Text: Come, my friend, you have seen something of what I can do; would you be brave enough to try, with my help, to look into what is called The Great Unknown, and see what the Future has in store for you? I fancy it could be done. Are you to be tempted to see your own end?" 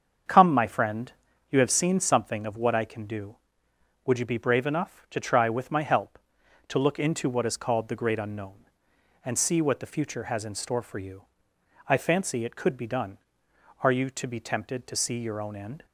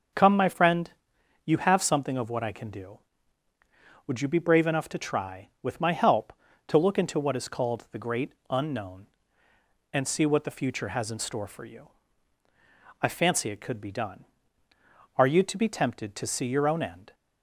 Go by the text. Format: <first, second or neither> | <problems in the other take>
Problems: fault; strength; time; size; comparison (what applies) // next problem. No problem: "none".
first | starts louder than the rest; until 1.6 s; 6.5 dB; strong in the first // skips "seen"; at 1.8 s // pauses between "Great" and "Unknown"; slight; at 8.3 s; 0.16 s long